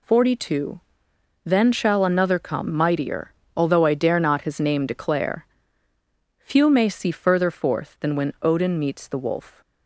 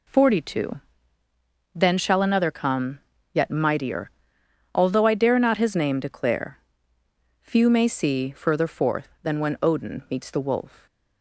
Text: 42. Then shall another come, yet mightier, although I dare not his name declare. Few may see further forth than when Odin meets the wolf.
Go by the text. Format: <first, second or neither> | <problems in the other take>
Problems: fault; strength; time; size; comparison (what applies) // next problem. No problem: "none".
second | skips "yet"; at 2.7 s